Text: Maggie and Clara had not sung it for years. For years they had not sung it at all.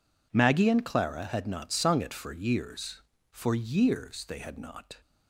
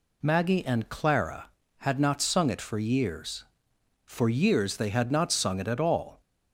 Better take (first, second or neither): second